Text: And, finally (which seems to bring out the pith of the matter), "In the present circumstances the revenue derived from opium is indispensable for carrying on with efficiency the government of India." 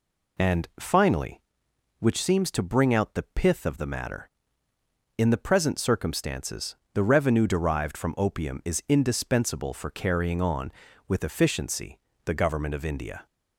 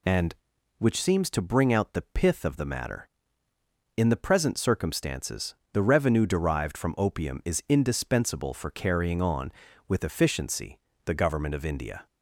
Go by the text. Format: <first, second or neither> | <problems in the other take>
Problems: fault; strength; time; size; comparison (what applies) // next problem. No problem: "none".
first | skips "finally"; at 0.5 s // pauses between "circumstances" and "the"; slight; at 5.5 s; 0.18 s long; slight in the first // pauses between "efficiency" and "the"; slight; at 10.7 s; 0.26 s long; slight in the first